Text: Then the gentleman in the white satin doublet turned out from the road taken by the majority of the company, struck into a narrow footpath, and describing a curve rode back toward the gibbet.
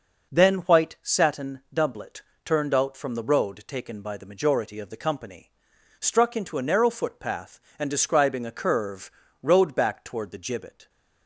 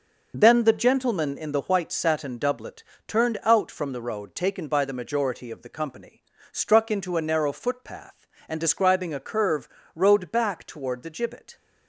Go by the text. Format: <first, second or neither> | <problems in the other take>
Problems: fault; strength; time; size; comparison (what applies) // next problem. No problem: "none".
second | skips "the gentleman in the"; at 0.5 s // pauses between "doublet" and "turned"; slight; at 2.2 s; 0.24 s long; slight in the second // pauses between "curve" and "rode"; slight; at 9.1 s; 0.30 s long; slight in the second